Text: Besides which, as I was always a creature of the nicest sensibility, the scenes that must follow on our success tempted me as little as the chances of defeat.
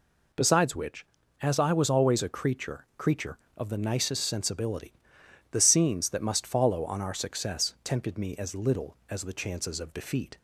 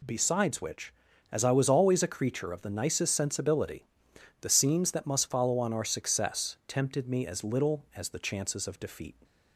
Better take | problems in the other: second | says "creature" twice; at 2.9 s

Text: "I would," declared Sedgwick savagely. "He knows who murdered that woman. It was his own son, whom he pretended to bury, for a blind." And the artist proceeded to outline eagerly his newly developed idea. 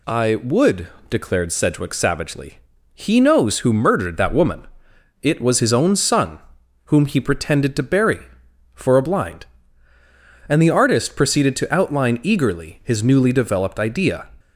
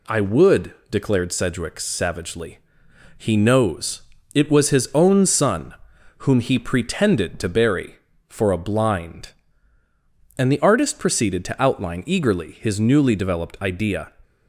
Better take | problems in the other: first | skips "who murdered that woman"; at 4.1 s

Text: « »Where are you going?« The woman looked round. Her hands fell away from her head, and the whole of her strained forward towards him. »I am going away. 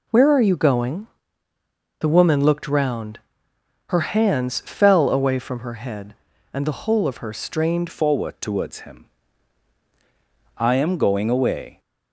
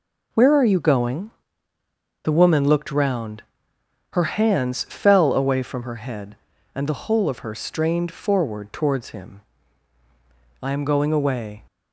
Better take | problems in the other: second | changes voice at "forward"; from 7.9 s on; 3.9 s long

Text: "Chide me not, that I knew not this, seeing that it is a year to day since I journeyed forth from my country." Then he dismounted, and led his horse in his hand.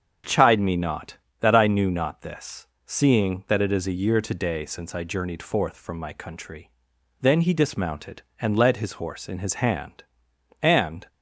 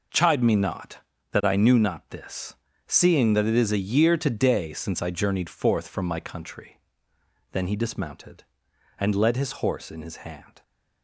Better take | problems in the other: second | starts louder than the rest; strong; until 1.4 s; 8 dB // goes on to say "And"; slight; from 10.6 s on; 0.46 s long

